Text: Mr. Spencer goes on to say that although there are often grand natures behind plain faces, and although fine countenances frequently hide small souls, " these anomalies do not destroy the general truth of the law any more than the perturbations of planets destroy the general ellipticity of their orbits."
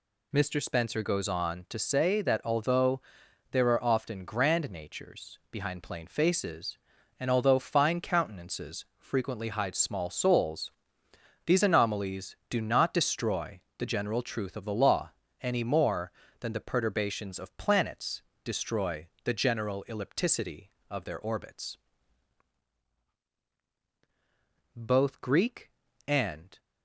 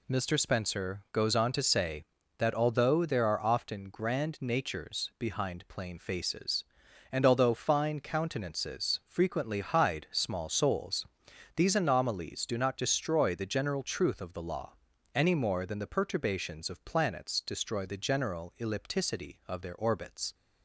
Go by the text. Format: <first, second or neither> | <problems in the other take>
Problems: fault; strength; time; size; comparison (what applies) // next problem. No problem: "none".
second | pauses between "although" and "there"; noticeable; at 3.0 s; 0.50 s long // pauses between "destroy" and "the"; slight; at 13.6 s; 0.16 s long // pauses between "law" and "any"; slight; at 15.1 s; 0.30 s long; also in the second // pauses between "planets" and "destroy"; slight; at 18.2 s; 0.22 s long // pauses between "destroy" and "the"; slight; at 19.0 s; 0.16 s long // goes on to say "Both Greek and"; strong; from 24.7 s on; 1.8 s long